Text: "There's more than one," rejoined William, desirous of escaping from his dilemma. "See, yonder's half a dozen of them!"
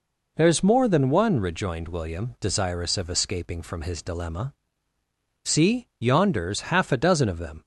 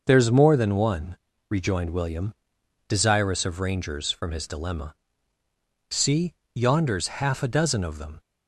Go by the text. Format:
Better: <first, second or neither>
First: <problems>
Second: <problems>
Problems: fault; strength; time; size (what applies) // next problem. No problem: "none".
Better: first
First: none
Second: says "rangers" for "escaping"; at 3.5 s